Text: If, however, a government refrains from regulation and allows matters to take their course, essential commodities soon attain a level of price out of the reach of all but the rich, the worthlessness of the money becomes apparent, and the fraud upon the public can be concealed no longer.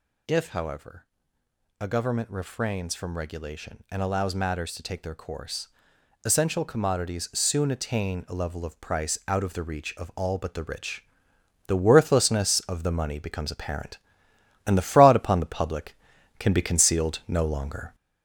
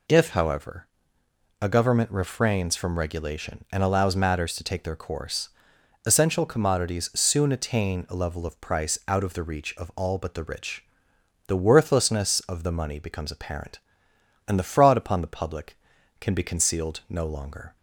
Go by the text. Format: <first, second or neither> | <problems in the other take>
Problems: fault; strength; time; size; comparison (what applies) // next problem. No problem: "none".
second | gets louder; noticeable; throughout; 5 dB